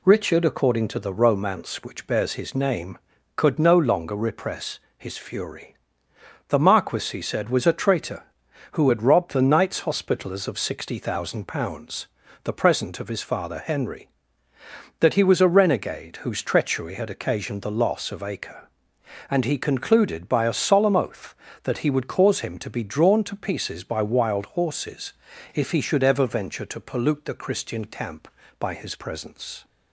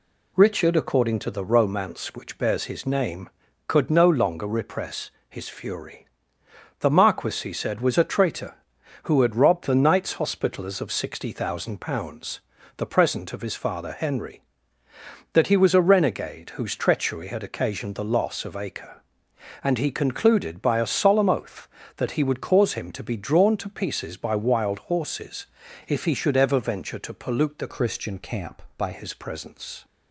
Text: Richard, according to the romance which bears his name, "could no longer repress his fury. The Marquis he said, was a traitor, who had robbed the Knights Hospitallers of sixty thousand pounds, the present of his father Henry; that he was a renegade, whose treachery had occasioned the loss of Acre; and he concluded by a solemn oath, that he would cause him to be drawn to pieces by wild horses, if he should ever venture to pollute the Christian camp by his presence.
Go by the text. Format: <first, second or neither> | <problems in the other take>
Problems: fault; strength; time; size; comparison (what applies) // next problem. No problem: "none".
first | pauses between "repress" and "his"; slight; at 5.1 s; 0.18 s long; slight in the first // changes voice from "Christian" to "by"; from 27.6 to 28.9 s; 1.3 s long